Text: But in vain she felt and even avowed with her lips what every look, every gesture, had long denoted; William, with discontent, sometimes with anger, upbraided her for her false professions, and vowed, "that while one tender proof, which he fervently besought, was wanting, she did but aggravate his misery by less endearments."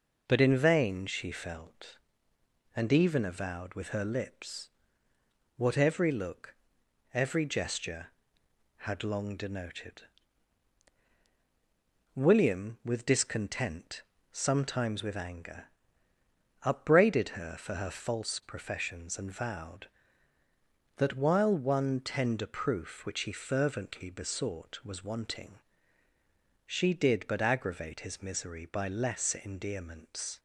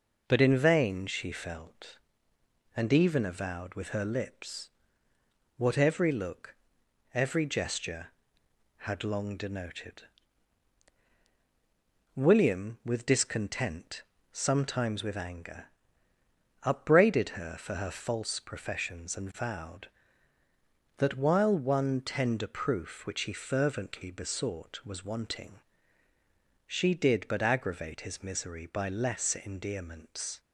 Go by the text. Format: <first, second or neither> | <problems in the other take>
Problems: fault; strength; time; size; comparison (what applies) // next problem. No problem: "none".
neither | pauses between "lips" and "what"; noticeable; the same in both